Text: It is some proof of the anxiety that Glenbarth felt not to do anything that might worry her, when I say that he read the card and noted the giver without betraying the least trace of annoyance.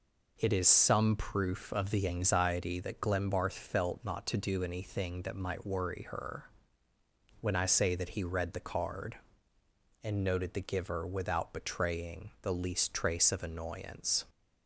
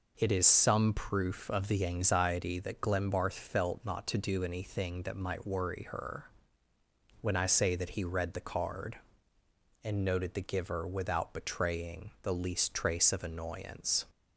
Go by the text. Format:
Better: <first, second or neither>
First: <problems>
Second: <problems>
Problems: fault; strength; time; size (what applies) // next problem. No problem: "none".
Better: neither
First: none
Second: none